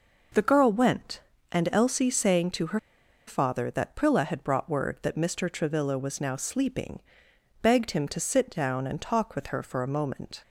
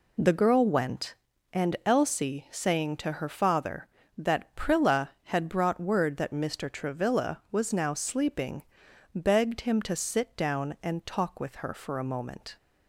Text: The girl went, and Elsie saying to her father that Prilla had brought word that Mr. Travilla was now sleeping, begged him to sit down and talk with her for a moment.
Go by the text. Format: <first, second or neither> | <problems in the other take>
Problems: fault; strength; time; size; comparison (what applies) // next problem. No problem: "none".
second | pauses between "her" and "father"; noticeable; at 2.7 s; 0.48 s long